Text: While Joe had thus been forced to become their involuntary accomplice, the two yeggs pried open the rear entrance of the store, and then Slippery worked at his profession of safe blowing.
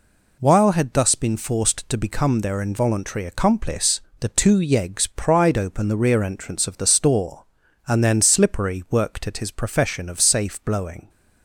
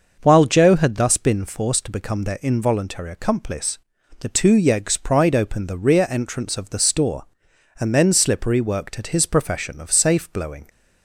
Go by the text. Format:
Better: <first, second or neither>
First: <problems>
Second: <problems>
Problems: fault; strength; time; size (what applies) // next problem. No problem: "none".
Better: second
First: skips "Joe"; at 0.7 s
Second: none